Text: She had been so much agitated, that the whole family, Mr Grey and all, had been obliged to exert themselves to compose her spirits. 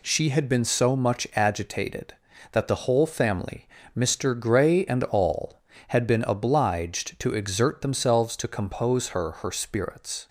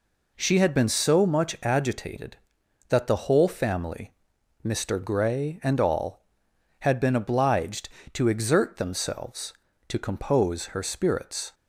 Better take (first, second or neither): second